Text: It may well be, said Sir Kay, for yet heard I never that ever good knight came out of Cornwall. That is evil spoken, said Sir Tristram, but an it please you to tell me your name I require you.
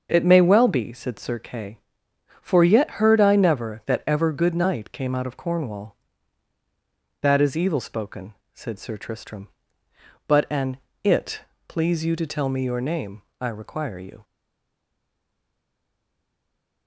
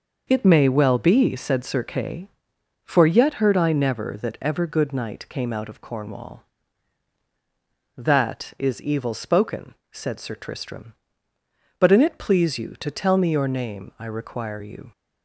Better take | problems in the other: second | starts louder than the rest; until 1.1 s; 6.5 dB // pauses between "an" and "it"; slight; at 10.7 s; 0.26 s long // pauses between "it" and "please"; slight; at 11.4 s; 0.26 s long // pauses between "name" and "I"; slight; at 13.2 s; 0.18 s long // stays silent after the last word; strong; from 14.2 s on; 2.6 s long

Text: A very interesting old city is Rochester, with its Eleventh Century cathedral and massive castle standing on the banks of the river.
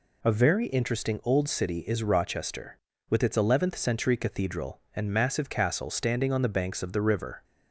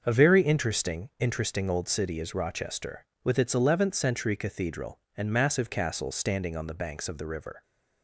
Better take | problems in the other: first | starts louder than the rest; until 1.0 s; 6.5 dB // says "interesting" twice; at 1.1 s

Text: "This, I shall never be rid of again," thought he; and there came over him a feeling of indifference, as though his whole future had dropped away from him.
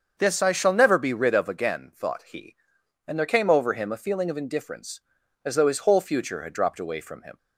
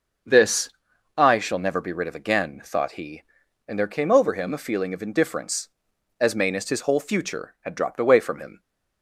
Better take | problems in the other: first | starts louder than the rest; until 1.7 s; 6.5 dB; also in the first // says "mainest" for "though"; at 6.3 s

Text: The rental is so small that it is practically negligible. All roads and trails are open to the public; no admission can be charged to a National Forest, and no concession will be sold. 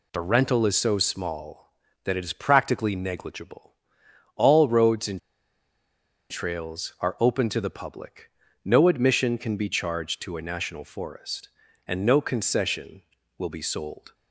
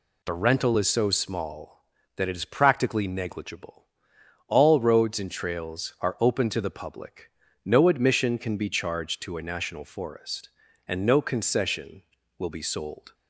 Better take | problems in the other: second | pauses between "and" and "trails"; at 5.1 s; 1.1 s long

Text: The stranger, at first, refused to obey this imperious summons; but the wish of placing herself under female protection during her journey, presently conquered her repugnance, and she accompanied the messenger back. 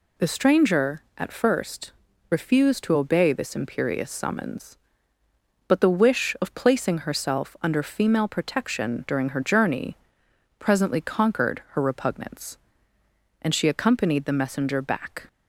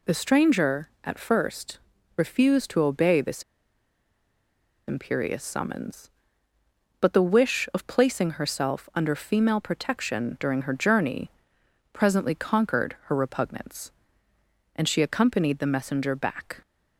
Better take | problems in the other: first | pauses between "this" and "imperious"; strong; at 3.4 s; 1.4 s long

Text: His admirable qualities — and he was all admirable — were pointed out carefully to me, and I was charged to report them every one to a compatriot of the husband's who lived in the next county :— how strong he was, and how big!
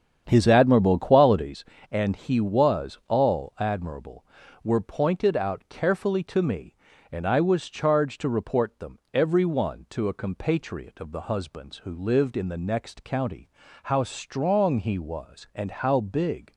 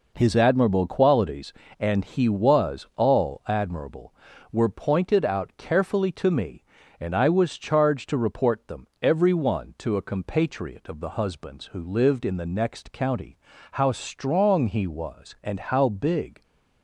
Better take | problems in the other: second | starts louder than the rest; strong; until 1.5 s; 8 dB

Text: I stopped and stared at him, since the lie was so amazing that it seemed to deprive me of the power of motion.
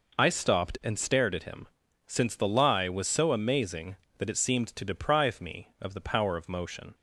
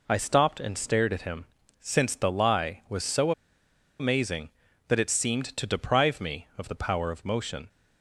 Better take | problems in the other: first | pauses between "so" and "amazing"; noticeable; at 3.3 s; 0.68 s long

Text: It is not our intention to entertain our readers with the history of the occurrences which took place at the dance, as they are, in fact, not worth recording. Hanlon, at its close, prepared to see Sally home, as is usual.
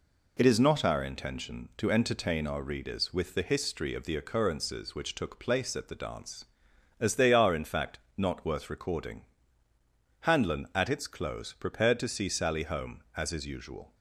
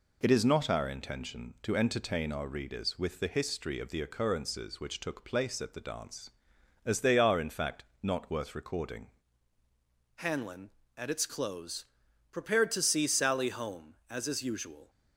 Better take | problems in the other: first | changes voice at "Hanlon"; from 10.1 s on; 4.7 s long

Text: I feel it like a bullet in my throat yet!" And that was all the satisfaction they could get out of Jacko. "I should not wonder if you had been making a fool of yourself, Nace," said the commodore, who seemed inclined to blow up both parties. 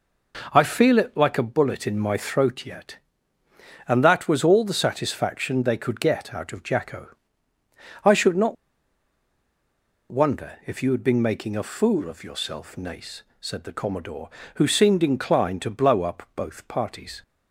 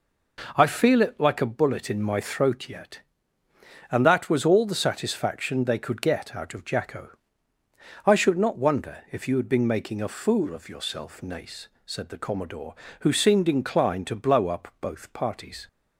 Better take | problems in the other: second | pauses between "not" and "wonder"; strong; at 8.5 s; 1.5 s long

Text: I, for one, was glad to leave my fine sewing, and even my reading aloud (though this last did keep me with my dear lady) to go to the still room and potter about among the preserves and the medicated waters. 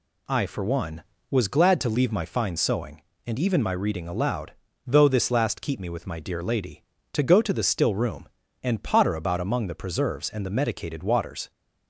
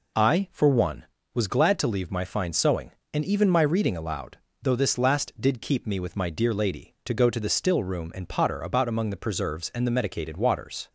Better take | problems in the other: second | skips "did"; at 5.5 s

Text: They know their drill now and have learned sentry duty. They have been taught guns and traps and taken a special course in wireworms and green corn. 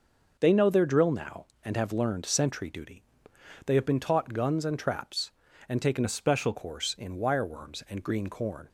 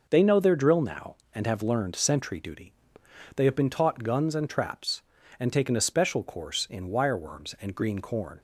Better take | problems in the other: second | starts louder than the rest; noticeable; until 1.4 s; 6 dB // changes voice from "a" to "special"; from 6.0 to 6.5 s; 0.5 s long

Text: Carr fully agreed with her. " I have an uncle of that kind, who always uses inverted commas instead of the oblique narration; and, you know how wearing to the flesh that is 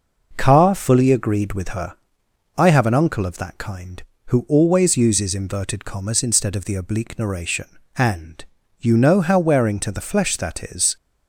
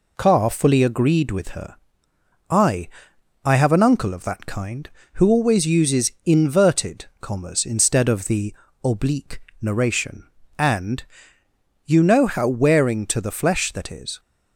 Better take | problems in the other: first | says "I" twice; at 3.4 s // pauses between "the" and "oblique"; slight; at 8.5 s; 0.30 s long // pauses between "oblique" and "narration"; slight; at 9.4 s; 0.18 s long

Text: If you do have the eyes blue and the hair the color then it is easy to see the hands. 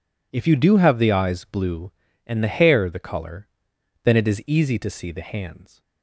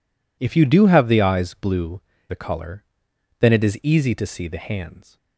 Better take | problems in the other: first | skips "and the hair"; at 2.1 s // pauses between "color" and "then"; noticeable; at 2.8 s; 0.58 s long; noticeable in the first

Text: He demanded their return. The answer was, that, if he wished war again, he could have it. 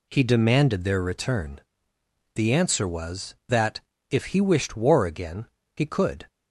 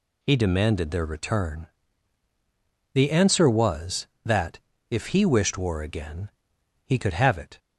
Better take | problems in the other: second | stops before "have it"; at 6.2 s

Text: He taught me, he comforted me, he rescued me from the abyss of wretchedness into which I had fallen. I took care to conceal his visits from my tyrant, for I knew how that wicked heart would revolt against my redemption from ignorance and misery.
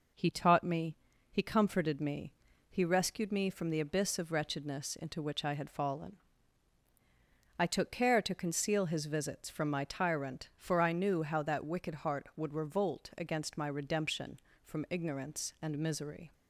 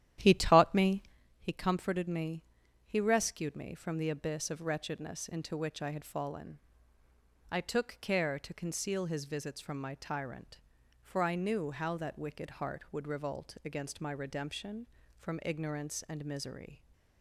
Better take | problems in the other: first | starts louder than the rest; strong; until 1.2 s; 11.5 dB

